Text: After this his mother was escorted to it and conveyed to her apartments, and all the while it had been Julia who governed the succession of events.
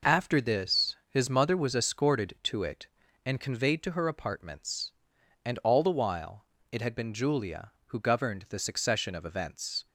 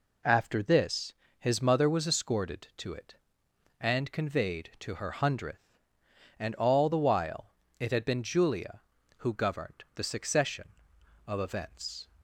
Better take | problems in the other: first | pauses between "this" and "his"; slight; at 1.1 s; 0.26 s long // says "hundredth" for "apartments"; at 5.1 s // pauses between "while" and "it"; slight; at 7.5 s; 0.26 s long; slight in the first

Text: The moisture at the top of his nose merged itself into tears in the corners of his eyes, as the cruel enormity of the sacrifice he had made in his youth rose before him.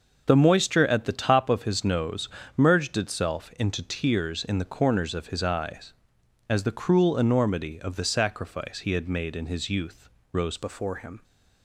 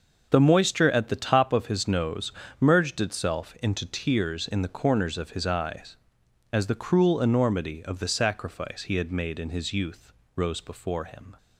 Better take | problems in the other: second | starts louder than the rest; noticeable; until 1.2 s; 6 dB // pauses between "nose" and "merged"; slight; at 2.2 s; 0.26 s long; slight in the second // pauses between "youth" and "rose"; slight; at 10.0 s; 0.24 s long; slight in the second // changes voice at "before"; from 10.5 s on; 0.7 s long

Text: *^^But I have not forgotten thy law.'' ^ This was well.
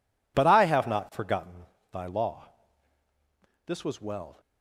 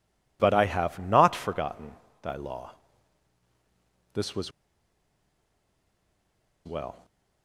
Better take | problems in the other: first | pauses between "forgotten" and "thy"; slight; at 1.9 s; 0.32 s long; slight in the first // pauses between "was" and "well"; strong; at 4.5 s; 2.1 s long

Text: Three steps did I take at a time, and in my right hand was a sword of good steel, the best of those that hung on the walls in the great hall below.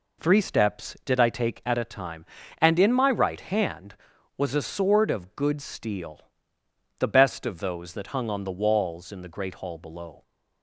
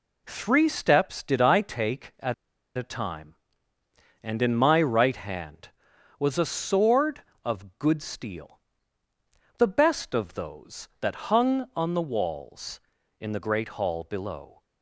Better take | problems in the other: first | pauses between "at" and "a"; at 2.3 s; 0.43 s long

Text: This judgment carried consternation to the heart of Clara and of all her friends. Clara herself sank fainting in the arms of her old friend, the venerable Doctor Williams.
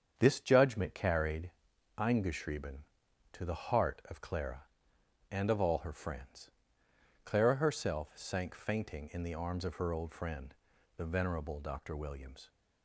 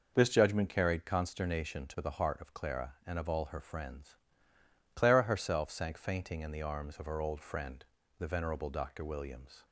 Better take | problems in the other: second | starts louder than the rest; strong; until 1.1 s; 7.5 dB // says "eingeschrieben" for "consternation"; at 1.9 s

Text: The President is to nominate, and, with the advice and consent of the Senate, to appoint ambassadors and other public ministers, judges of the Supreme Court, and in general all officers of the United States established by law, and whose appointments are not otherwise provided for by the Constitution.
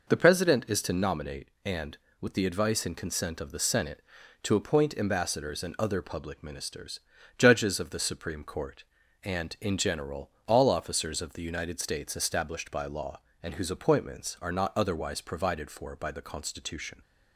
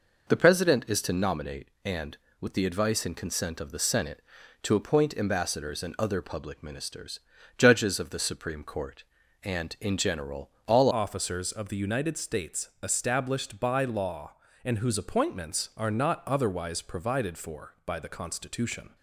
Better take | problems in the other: first | pauses between "general" and "all"; slight; at 10.5 s; 0.16 s long; slight in the first // changes voice at "officers"; from 10.9 s on; 8.0 s long

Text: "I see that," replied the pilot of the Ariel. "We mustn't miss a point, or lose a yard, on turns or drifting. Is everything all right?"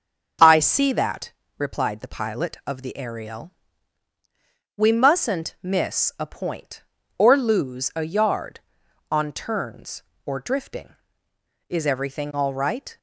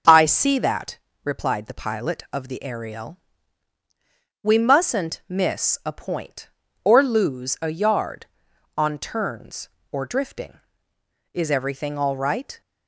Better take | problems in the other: neither | starts louder than the rest; the same in both

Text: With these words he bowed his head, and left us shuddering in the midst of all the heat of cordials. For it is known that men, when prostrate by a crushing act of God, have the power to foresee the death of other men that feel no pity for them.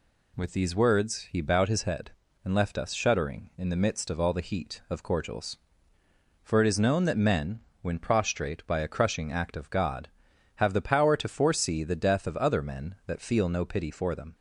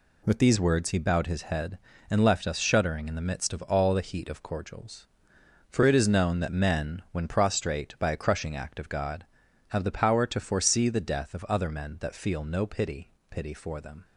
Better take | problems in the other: first | says "pity" twice; at 13.2 s

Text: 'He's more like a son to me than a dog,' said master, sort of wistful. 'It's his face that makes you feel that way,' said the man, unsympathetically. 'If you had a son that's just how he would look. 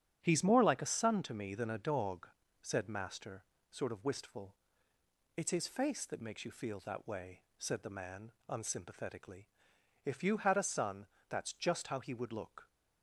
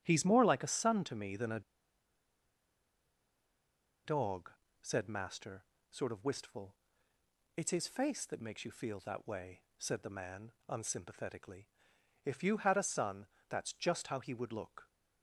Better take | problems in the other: first | starts louder than the rest; strong; until 1.0 s; 9 dB; strong in the first // pauses between "a" and "dog"; strong; at 1.6 s; 2.4 s long // pauses between "son" and "that's"; slight; at 13.2 s; 0.20 s long; slight in the first

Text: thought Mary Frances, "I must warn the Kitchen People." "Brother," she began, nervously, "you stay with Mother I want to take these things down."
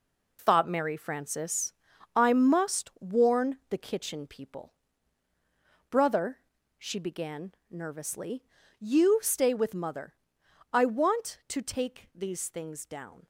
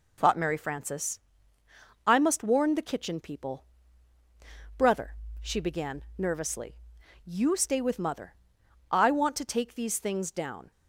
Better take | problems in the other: second | gets quieter; strong; throughout; 8.5 dB // pauses between "Mother" and "I"; noticeable; at 10.1 s; 0.56 s long; noticeable in the second

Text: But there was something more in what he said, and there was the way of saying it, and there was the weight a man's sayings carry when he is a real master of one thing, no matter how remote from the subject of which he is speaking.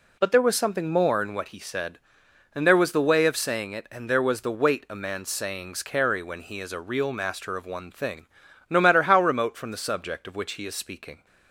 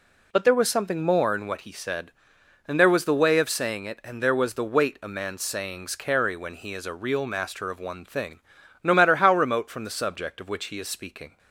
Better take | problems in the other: neither | none

